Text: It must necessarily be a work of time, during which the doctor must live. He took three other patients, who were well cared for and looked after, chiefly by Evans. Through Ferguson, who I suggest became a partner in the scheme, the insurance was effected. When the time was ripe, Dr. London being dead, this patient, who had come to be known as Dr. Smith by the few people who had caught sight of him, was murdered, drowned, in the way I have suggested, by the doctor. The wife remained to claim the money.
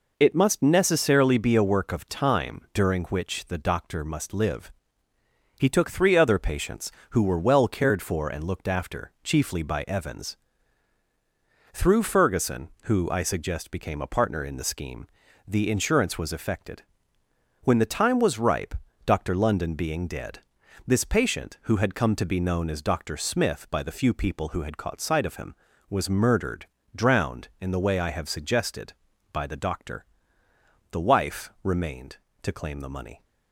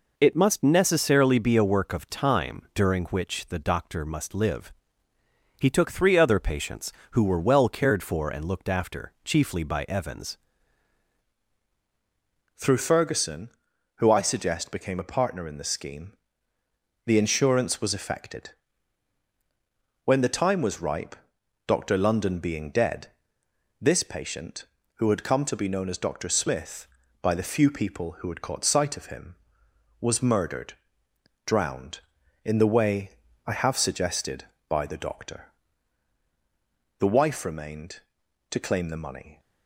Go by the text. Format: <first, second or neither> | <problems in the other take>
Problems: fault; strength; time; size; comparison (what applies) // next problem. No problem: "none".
first | changes voice at "Through"; from 12.5 s on; 26.8 s long // pauses between "way" and "I"; slight; at 33.1 s; 0.34 s long